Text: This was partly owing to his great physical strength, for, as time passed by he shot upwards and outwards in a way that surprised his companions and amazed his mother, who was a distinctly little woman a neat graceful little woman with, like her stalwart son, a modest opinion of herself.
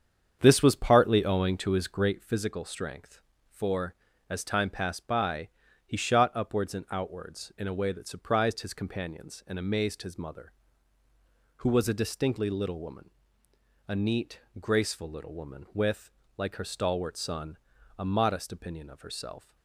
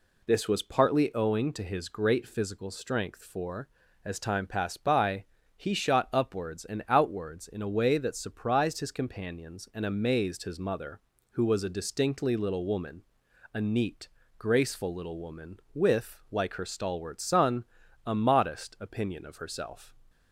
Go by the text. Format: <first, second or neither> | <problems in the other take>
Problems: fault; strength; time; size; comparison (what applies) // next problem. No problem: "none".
second | starts louder than the rest; strong; until 2.2 s; 7.5 dB // pauses between "by" and "he"; slight; at 5.4 s; 0.36 s long; slight in the second // pauses between "woman" and "a"; noticeable; at 13.0 s; 0.80 s long; noticeable in the second // pauses between "neat" and "graceful"; slight; at 14.3 s; 0.22 s long; slight in the second